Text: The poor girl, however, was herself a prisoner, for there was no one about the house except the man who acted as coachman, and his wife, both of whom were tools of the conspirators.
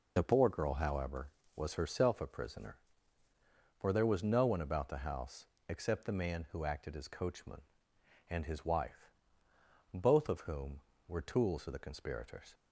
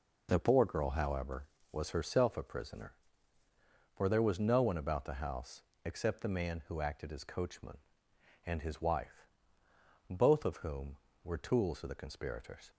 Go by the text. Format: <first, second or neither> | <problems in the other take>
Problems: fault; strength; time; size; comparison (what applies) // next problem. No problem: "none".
second | loses the start of "The"; at 0.1 s; 35 ms // pauses between "house" and "except"; slight; at 5.4 s; 0.20 s long; slight in the second